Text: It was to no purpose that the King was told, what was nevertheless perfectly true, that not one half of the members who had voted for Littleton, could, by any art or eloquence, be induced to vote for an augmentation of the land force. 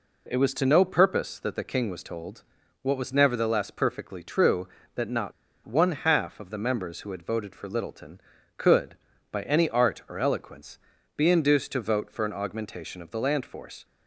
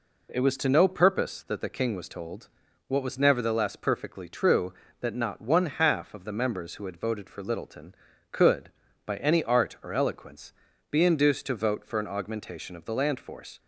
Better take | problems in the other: second | pauses between "not" and "one"; slight; at 5.3 s; 0.34 s long

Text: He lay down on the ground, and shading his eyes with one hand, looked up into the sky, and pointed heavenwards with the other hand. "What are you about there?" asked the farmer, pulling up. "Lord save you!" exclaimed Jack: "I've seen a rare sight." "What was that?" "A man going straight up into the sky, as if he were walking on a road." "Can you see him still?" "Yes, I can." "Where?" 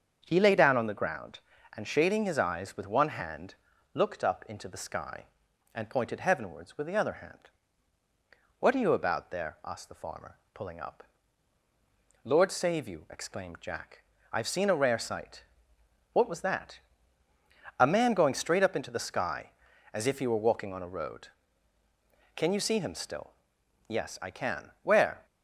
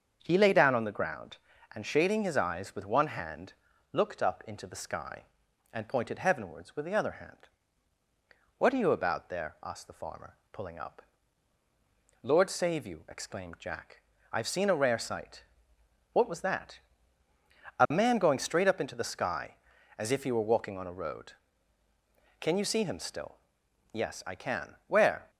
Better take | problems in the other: neither | starts louder than the rest; the same in both

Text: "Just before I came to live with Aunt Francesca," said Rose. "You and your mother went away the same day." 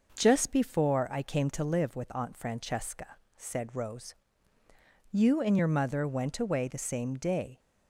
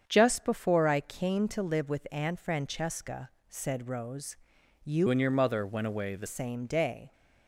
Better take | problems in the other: first | starts louder than the rest; strong; until 1.0 s; 7.5 dB // changes voice from "and" to "the"; from 5.0 to 6.2 s; 1.2 s long

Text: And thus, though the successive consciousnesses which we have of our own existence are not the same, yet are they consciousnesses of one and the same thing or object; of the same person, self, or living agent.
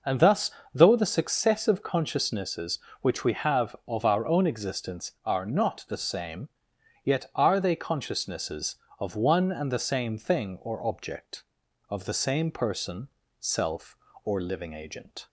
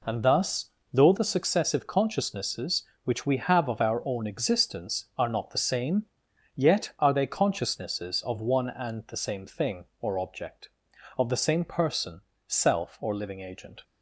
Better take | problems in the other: neither | none

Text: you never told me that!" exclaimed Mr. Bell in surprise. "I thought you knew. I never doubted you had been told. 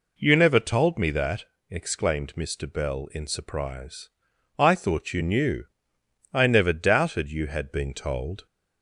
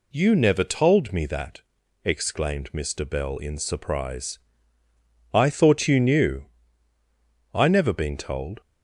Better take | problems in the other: first | skips "doubted you had"; at 7.9 s

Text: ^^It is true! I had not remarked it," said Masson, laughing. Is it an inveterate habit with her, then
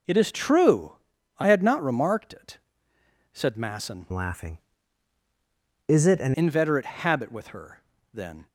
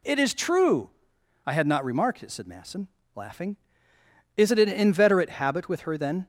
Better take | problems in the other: second | changes voice from "laughing" to "an"; from 4.1 to 6.3 s; 2.2 s long

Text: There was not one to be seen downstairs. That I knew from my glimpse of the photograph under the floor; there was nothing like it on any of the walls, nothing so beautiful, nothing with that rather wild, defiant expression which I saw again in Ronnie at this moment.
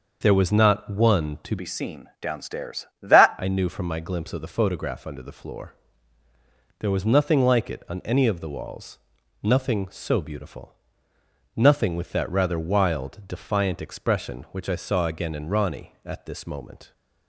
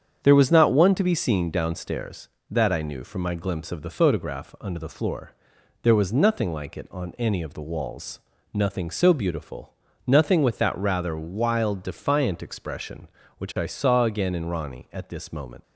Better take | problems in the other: second | starts louder than the rest; until 1.2 s; 6.5 dB; strong in the second // changes voice from "be" to "That"; from 1.5 to 3.3 s; 1.8 s long

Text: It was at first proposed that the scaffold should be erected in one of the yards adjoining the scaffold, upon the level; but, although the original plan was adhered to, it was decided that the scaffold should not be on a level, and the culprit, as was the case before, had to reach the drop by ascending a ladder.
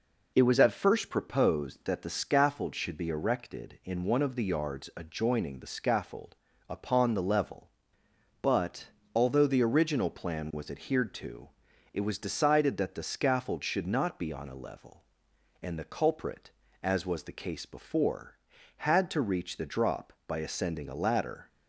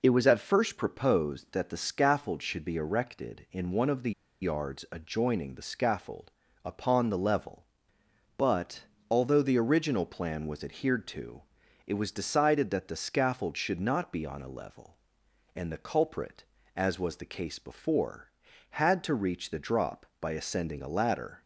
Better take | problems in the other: first | pauses between "the" and "yards"; slight; at 4.1 s; 0.30 s long

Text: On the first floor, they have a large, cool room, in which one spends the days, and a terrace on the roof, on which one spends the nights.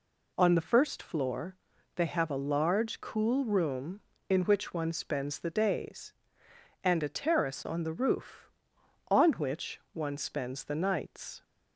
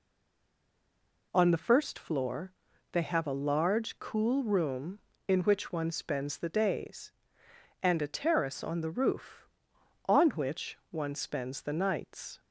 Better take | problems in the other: first | stays silent before the first word; noticeable; until 1.3 s; 1.3 s long

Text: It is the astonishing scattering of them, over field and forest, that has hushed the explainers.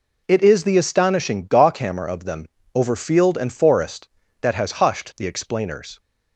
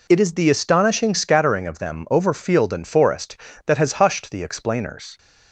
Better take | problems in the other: second | says "gawkhammer" for "scattering"; at 1.4 s

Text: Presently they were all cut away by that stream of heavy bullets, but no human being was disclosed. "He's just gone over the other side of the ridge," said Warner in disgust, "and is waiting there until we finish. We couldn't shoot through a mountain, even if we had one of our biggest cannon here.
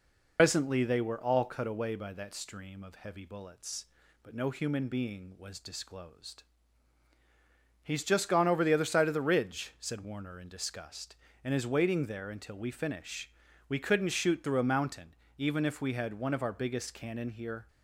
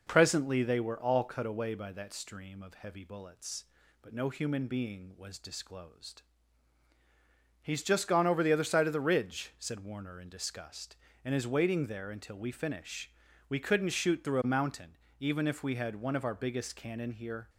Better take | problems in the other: second | loses the start of "Presently"; at 0.3 s; 110 ms

